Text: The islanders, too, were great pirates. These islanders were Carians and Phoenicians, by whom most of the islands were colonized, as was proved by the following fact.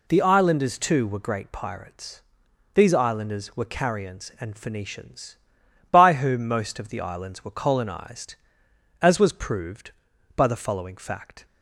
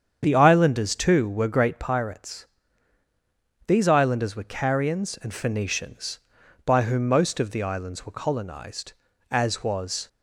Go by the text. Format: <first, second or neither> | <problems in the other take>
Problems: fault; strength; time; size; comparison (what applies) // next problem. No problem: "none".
first | starts louder than the rest; strong; until 1.2 s; 8 dB // stops before "proved by the following fact"; at 10.0 s